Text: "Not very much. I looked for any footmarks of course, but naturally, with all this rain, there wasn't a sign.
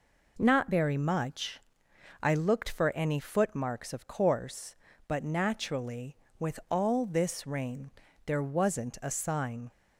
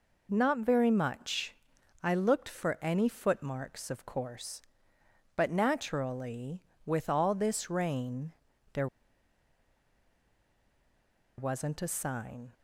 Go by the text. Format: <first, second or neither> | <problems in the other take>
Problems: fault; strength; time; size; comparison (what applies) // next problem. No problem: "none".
first | pauses between "there" and "wasn't"; strong; at 8.8 s; 2.5 s long